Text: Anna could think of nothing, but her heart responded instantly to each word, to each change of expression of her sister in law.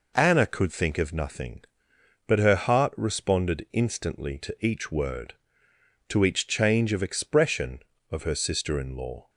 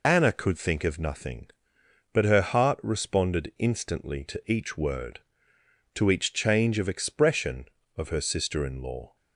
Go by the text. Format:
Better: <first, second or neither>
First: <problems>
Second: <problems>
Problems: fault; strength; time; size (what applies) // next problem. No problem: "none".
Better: first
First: none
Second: loses the start of "Anna"; at 0.0 s; 40 ms